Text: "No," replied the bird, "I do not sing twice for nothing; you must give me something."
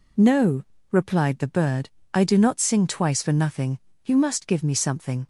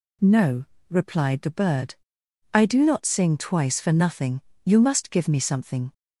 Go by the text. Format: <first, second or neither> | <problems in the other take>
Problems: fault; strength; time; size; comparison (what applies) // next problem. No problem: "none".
neither | none